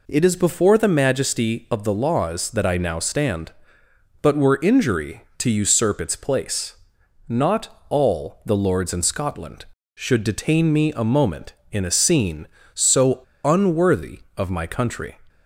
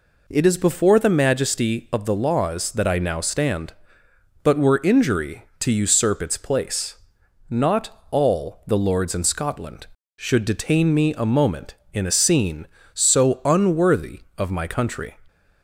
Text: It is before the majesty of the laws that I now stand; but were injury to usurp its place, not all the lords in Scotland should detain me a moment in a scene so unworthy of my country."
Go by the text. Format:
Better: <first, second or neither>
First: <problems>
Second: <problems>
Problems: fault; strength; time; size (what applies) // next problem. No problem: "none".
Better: second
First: pauses between "so" and "unworthy"; slight; at 13.1 s; 0.25 s long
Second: none